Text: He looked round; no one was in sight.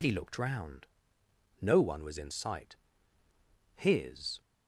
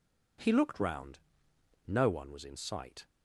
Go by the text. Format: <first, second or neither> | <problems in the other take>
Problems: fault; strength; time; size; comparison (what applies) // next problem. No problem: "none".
second | goes on to say "His"; noticeable; from 3.7 s on; 0.64 s long